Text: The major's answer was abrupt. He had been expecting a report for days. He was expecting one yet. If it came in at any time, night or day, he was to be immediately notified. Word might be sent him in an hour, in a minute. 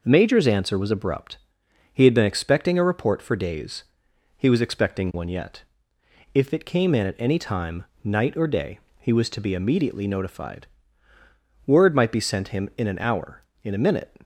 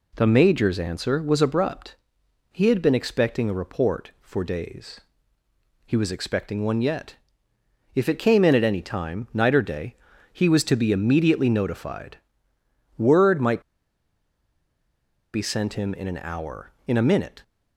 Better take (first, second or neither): first